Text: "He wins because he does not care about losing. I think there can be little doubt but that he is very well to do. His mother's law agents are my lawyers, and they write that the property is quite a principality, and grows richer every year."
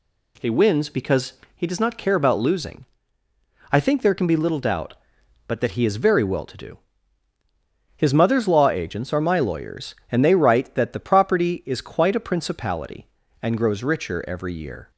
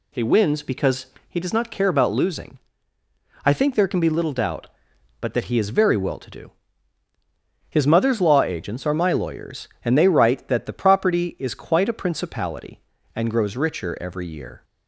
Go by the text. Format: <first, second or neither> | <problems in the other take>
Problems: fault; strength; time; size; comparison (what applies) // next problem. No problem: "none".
first | loses the start of "He"; at 0.1 s; 40 ms // pauses between "because" and "he"; slight; at 1.0 s; 0.20 s long; slight in the first